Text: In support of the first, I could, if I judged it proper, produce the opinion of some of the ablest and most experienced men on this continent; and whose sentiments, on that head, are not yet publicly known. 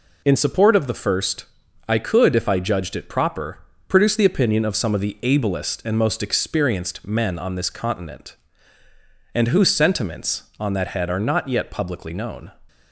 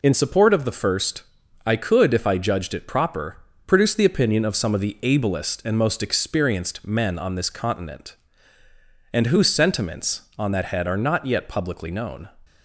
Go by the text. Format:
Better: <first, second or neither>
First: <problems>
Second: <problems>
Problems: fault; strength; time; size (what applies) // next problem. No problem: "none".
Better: neither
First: none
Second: none